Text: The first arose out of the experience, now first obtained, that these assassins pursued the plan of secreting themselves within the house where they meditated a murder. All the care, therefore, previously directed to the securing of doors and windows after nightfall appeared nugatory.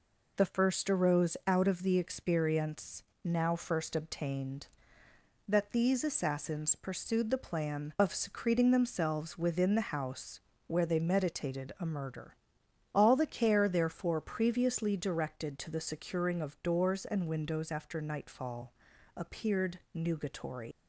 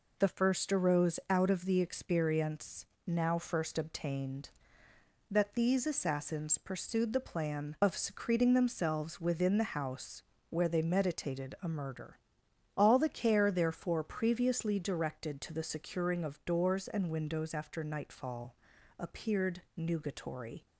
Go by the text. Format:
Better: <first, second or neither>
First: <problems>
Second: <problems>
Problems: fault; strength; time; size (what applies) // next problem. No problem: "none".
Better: second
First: pauses between "house" and "where"; slight; at 10.3 s; 0.26 s long // pauses between "nightfall" and "appeared"; at 18.7 s; 0.42 s long // leaves "nugatory" unfinished; at 20.7 s; 115 ms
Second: pauses between "house" and "where"; slight; at 10.2 s; 0.26 s long // pauses between "nightfall" and "appeared"; at 18.5 s; 0.42 s long